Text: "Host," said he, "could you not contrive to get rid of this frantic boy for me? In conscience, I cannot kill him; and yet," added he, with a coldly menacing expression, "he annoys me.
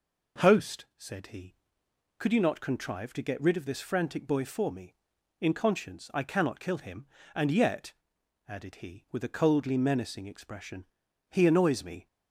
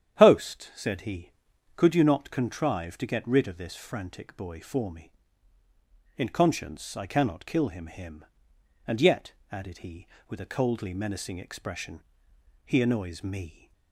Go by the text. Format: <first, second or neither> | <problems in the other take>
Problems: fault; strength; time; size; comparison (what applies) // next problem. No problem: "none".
first | starts louder than the rest; strong; until 1.2 s; 9.5 dB // says "him" twice; at 7.8 s